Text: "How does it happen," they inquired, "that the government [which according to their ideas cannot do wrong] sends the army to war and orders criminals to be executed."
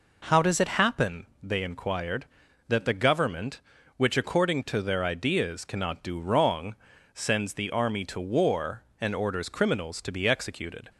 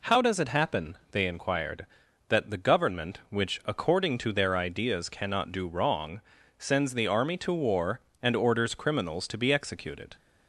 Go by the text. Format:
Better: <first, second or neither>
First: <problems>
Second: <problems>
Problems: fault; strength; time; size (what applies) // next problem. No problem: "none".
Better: neither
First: pauses between "wrong" and "sends"; at 6.7 s; 0.40 s long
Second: pauses between "wrong" and "sends"; slight; at 6.2 s; 0.36 s long